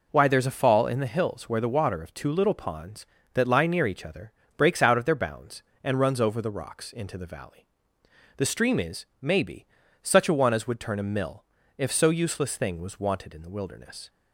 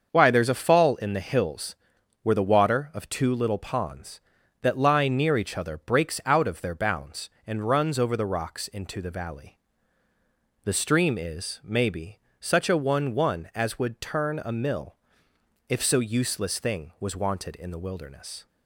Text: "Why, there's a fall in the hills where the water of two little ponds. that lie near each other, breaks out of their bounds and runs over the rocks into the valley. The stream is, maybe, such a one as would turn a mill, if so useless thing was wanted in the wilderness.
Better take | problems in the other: first | starts louder than the rest; until 1.1 s; 6.5 dB // pauses between "hills" and "where"; noticeable; at 1.7 s; 0.46 s long // says "one" twice; at 13.1 s

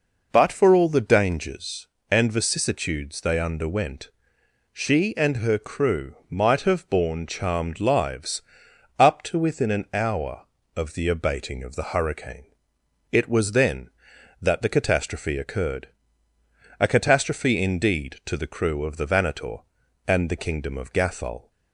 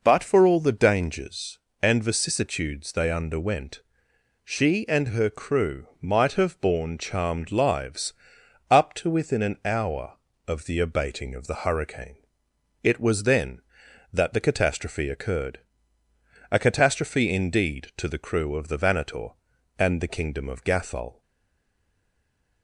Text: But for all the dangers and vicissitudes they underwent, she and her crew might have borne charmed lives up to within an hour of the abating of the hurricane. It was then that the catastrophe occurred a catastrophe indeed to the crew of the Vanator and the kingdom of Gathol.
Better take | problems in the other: first | pauses between "lives" and "up"; noticeable; at 8.1 s; 0.56 s long; noticeable in the first // pauses between "occurred" and "a"; noticeable; at 15.5 s; 0.94 s long; noticeable in the first // stays silent after the last word; noticeable; from 21.2 s on; 1.4 s long

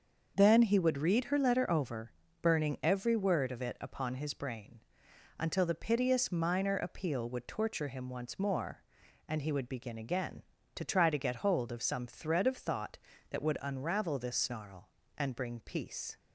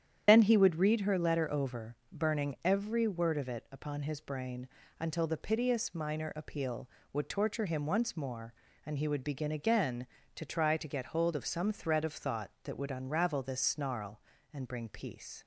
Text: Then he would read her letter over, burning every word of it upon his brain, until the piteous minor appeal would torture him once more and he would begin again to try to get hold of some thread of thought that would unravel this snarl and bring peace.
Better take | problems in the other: first | loses the start of "Then"; at 0.2 s; 50 ms // starts louder than the rest; strong; until 1.2 s; 9 dB; also in the first

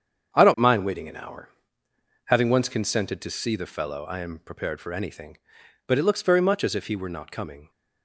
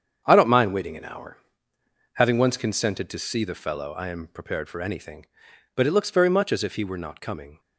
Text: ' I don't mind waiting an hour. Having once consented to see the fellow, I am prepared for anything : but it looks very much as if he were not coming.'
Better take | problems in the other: neither | starts louder than the rest; strong; the same in both

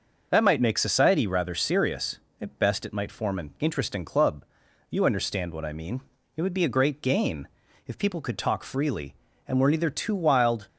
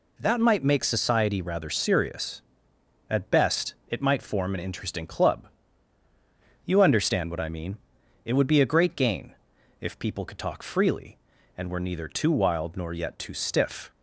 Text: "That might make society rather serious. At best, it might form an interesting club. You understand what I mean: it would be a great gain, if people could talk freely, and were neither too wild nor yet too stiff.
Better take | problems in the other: second | starts louder than the rest; noticeable; until 1.3 s; 6 dB // stops before "nor yet too stiff"; at 10.6 s

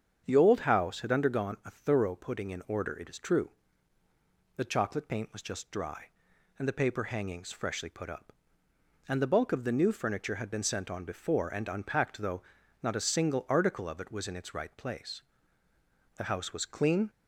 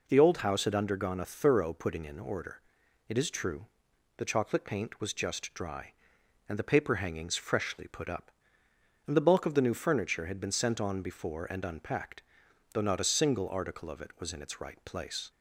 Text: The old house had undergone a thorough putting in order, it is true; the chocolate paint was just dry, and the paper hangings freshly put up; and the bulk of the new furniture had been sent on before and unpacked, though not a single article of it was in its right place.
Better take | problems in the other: second | starts louder than the rest; strong; until 1.2 s; 7.5 dB // pauses between "though" and "not"; at 12.4 s; 0.40 s long // goes on to say "The house was clean"; noticeable; from 16.1 s on; 0.94 s long

